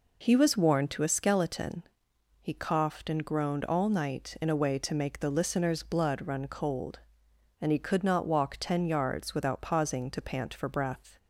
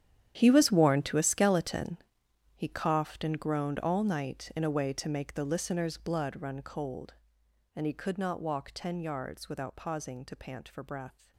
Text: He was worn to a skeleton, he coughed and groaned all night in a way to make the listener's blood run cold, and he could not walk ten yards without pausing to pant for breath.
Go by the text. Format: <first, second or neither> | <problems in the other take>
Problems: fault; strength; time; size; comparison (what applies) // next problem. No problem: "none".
first | gets quieter; strong; throughout; 17 dB